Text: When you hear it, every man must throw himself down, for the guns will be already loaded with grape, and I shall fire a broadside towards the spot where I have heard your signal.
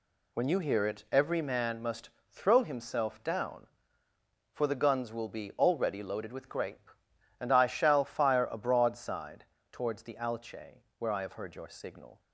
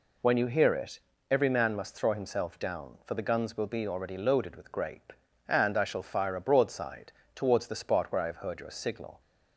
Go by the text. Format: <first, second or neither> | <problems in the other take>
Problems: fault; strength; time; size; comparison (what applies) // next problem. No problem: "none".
second | pauses between "must" and "throw"; slight; at 2.0 s; 0.18 s long // pauses between "broadside" and "towards"; slight; at 9.4 s; 0.26 s long; slight in the second // says "alche" for "spot"; at 10.1 s